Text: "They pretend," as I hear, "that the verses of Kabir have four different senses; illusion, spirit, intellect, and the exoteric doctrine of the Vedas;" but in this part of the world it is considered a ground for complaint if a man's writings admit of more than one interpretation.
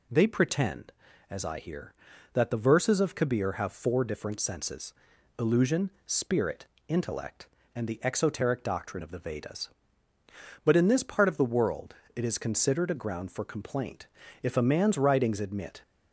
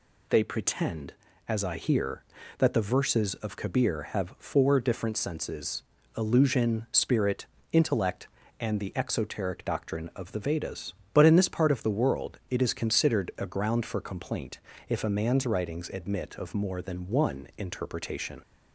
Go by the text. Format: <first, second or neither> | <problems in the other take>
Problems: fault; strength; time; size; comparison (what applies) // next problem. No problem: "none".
second | pauses between "world" and "it"; slight; at 11.9 s; 0.18 s long // pauses between "complaint" and "if"; slight; at 14.0 s; 0.36 s long; slight in the second // stops before "of more than one interpretation"; at 15.8 s